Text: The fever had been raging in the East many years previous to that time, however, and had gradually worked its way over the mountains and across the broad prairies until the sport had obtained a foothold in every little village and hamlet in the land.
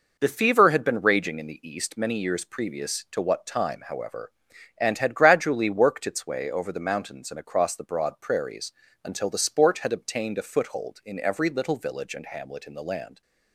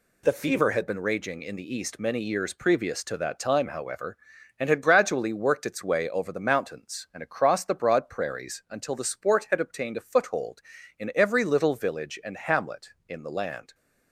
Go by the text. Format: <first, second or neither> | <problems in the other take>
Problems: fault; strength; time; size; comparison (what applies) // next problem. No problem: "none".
second | says "what" for "that"; at 3.2 s // pauses between "prairies" and "until"; slight; at 8.7 s; 0.32 s long